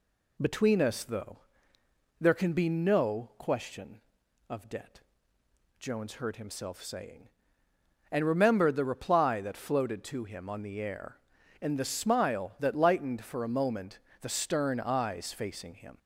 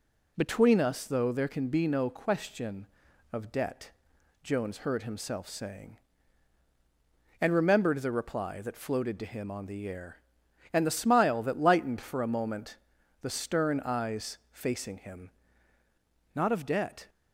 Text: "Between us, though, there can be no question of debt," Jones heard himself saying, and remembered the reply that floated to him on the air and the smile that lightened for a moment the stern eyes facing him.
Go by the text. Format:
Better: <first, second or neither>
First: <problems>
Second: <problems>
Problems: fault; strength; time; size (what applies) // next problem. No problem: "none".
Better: first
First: pauses between "moment" and "the"; slight; at 13.9 s; 0.22 s long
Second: pauses between "moment" and "the"; at 12.7 s; 0.44 s long // goes on to say "Not of debt"; noticeable; from 16.3 s on; 0.74 s long